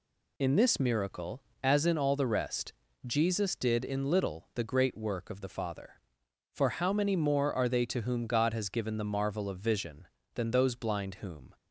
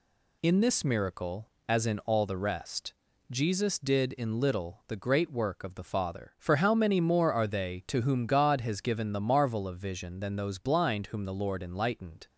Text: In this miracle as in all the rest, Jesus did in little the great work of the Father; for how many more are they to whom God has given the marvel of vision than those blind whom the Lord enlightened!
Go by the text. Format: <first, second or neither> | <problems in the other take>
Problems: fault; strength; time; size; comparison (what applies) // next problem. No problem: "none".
second | stops before "the Lord enlightened"; at 11.5 s